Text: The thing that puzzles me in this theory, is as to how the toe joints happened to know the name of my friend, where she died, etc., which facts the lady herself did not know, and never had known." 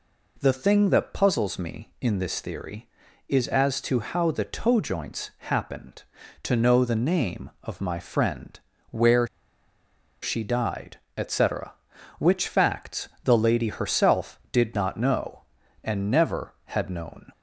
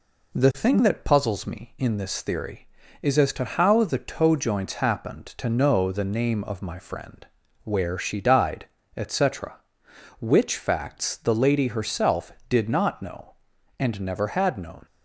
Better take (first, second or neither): second